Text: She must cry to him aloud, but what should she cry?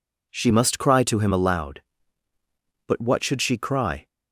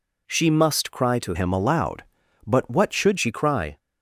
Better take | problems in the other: first | changes voice from "him" to "should"; from 1.3 to 3.1 s; 1.8 s long

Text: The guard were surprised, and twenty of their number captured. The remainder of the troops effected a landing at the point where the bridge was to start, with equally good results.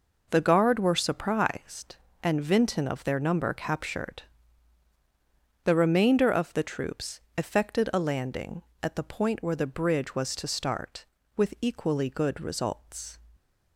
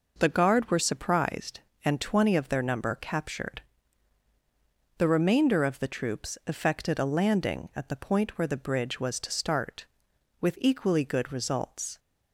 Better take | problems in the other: second | says "vinton" for "twenty"; at 2.4 s // pauses between "troops" and "effected"; slight; at 7.2 s; 0.16 s long

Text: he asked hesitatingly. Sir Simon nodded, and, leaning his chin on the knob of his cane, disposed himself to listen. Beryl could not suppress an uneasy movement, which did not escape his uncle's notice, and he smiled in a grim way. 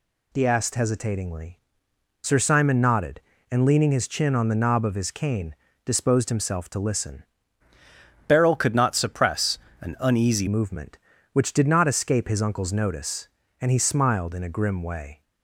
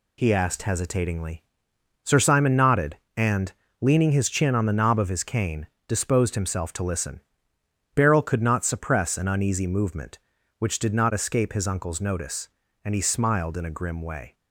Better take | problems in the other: second | changes voice from "Beryl" to "uneasy"; from 8.2 to 10.4 s; 2.2 s long // pauses between "suppress" and "an"; slight; at 9.5 s; 0.24 s long

